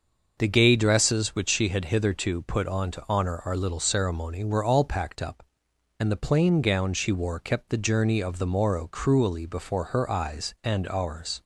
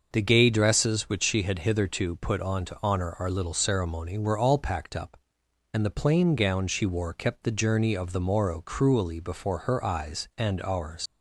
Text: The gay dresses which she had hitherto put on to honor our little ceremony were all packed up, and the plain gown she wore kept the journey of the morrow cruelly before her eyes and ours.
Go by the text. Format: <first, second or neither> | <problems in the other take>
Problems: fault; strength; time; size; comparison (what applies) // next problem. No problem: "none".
first | starts louder than the rest; until 1.1 s; 6 dB; also in the first // leaves "ours" unfinished; at 11.0 s; 105 ms